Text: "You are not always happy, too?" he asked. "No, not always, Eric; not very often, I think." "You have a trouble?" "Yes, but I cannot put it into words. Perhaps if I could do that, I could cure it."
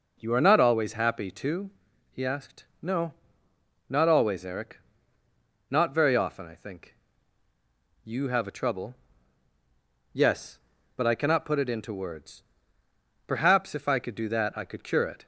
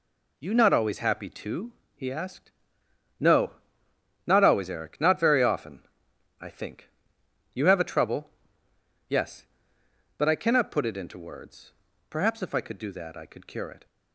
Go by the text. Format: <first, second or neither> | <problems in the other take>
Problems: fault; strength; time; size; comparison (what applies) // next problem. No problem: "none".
first | skips "are"; at 0.5 s